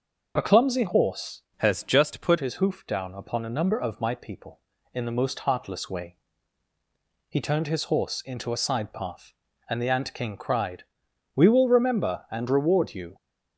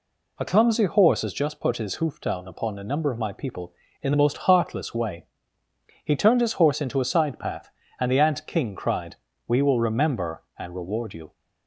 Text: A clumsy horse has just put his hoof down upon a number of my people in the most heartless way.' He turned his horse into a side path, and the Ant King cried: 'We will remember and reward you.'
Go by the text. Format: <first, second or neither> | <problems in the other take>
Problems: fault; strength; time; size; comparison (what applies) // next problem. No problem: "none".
second | starts louder than the rest; until 1.3 s; 6 dB // changes voice from "has" to "put"; from 1.5 to 2.3 s; 0.8 s long